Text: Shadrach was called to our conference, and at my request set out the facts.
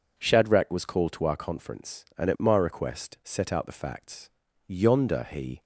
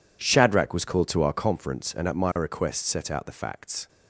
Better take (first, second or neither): second